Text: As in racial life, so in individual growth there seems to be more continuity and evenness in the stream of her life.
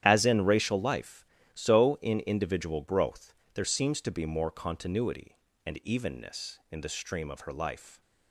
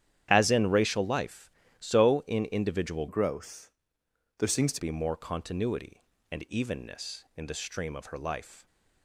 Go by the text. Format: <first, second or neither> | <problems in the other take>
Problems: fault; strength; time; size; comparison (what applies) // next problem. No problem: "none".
first | starts louder than the rest; strong; until 1.3 s; 10.5 dB; strong in the first // changes voice from "growth" to "to"; from 3.0 to 4.8 s; 1.8 s long // pauses between "growth" and "there"; noticeable; at 3.7 s; 0.66 s long; slight in the first